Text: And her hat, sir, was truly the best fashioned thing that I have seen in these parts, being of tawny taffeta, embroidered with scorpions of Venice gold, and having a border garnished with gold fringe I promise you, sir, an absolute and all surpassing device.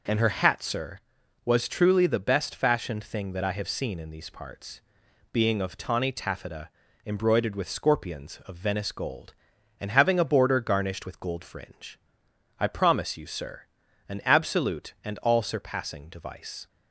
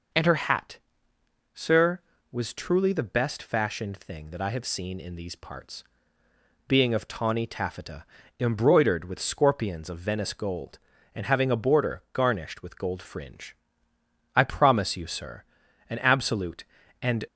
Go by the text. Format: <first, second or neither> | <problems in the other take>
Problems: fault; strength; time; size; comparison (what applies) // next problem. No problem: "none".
first | pauses between "fringe" and "I"; noticeable; at 13.5 s; 0.80 s long; noticeable in the first // stops before "all surpassing device"; at 17.2 s